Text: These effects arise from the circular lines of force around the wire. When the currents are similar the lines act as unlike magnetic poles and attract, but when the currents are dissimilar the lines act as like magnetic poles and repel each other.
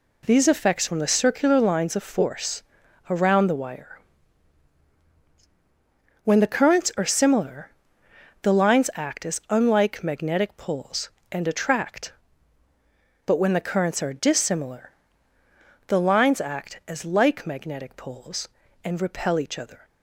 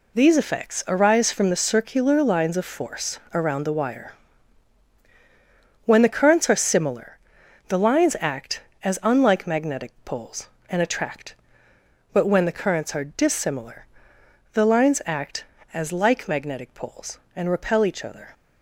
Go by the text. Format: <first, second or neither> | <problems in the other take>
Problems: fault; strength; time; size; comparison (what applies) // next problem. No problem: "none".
second | skips "arise"; at 0.8 s // pauses between "force" and "around"; noticeable; at 2.6 s; 0.48 s long // pauses between "similar" and "the"; noticeable; at 7.6 s; 0.74 s long; noticeable in the second // pauses between "dissimilar" and "the"; noticeable; at 14.9 s; 0.96 s long; noticeable in the second